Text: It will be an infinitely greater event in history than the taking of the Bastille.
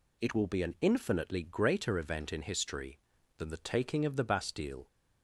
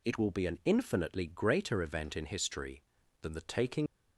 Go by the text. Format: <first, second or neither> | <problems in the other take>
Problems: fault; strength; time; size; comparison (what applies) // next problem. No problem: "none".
first | stops before "of the Bastille"; at 3.8 s